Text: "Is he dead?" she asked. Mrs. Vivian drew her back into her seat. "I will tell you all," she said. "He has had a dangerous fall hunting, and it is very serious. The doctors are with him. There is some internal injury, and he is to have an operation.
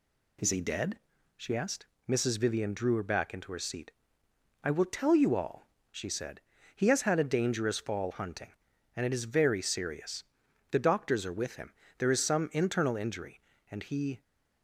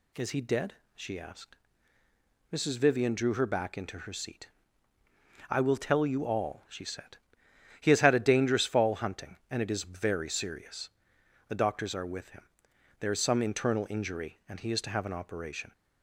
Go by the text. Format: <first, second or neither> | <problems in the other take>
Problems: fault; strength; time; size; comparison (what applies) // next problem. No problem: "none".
second | stops before "is to have an operation"; at 14.2 s